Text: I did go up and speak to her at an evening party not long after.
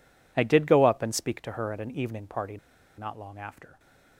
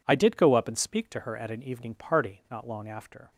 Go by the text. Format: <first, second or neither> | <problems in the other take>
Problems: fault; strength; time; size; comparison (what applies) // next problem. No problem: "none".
second | pauses between "party" and "not"; at 2.5 s; 0.41 s long